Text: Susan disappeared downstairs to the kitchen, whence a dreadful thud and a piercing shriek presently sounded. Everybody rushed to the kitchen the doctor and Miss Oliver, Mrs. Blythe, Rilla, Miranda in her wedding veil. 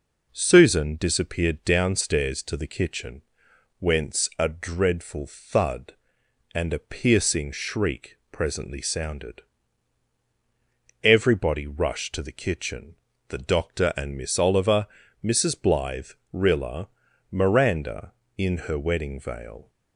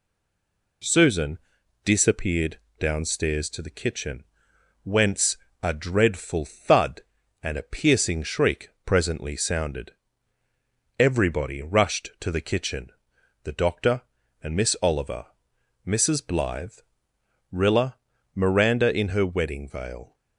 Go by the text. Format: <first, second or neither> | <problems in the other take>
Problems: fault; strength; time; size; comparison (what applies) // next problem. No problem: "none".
first | stays silent before the first word; slight; until 0.8 s; 0.8 s long // pauses between "Susan" and "disappeared"; noticeable; at 1.3 s; 0.46 s long // pauses between "disappeared" and "downstairs"; slight; at 2.5 s; 0.20 s long // pauses between "whence" and "a"; slight; at 5.3 s; 0.26 s long // pauses between "kitchen" and "the"; noticeable; at 12.9 s; 0.54 s long; slight in the first